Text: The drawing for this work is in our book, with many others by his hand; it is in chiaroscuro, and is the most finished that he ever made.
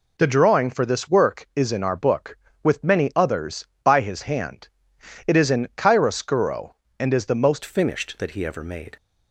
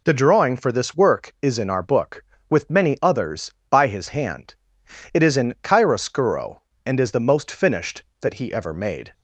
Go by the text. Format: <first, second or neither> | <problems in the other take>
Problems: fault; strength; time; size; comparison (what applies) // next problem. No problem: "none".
second | changes voice at "finished"; from 7.6 s on; 1.3 s long